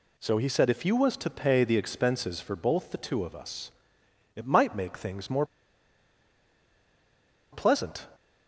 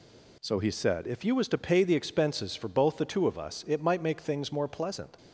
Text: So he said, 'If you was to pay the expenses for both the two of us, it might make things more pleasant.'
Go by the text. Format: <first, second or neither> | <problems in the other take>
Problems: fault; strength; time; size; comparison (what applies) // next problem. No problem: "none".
second | pauses between "more" and "pleasant"; strong; at 5.4 s; 2.0 s long